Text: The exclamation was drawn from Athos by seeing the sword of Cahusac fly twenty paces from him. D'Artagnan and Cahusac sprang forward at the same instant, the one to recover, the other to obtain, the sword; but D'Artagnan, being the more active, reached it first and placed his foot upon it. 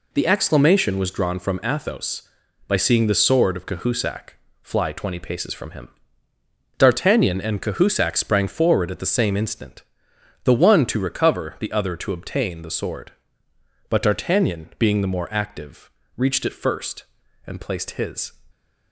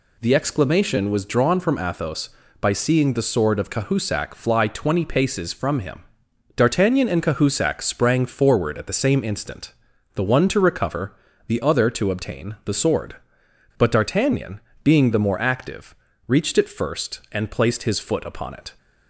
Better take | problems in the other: second | pauses between "Cahusac" and "fly"; slight; at 4.3 s; 0.30 s long // stops before "foot upon it"; at 18.5 s

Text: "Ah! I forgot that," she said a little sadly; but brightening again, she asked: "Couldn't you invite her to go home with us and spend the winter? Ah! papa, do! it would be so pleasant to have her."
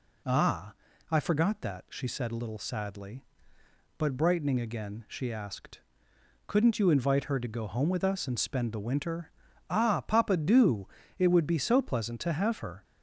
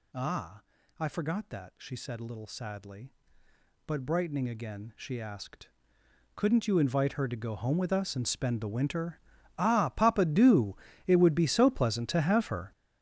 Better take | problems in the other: first | gets louder; strong; throughout; 12 dB

